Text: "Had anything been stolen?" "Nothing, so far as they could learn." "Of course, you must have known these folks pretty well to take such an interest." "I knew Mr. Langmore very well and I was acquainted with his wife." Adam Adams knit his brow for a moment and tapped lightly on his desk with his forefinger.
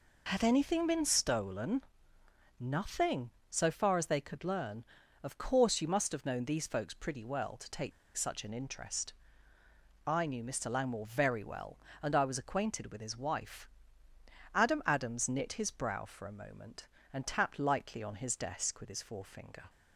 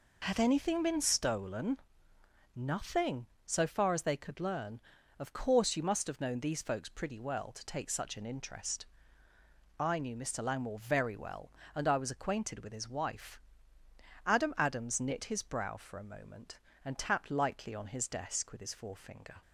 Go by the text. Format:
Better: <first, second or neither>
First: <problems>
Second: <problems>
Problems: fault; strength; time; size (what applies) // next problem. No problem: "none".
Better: second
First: pauses between "take" and "such"; slight; at 7.9 s; 0.25 s long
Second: none